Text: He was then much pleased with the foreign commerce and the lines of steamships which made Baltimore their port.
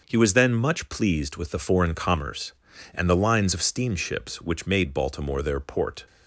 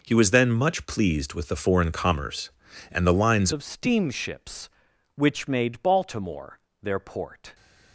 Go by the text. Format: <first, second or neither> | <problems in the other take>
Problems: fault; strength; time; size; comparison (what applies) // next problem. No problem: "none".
first | changes voice at "of"; from 3.5 s on; 4.0 s long // pauses between "Baltimore" and "their"; slight; at 6.5 s; 0.24 s long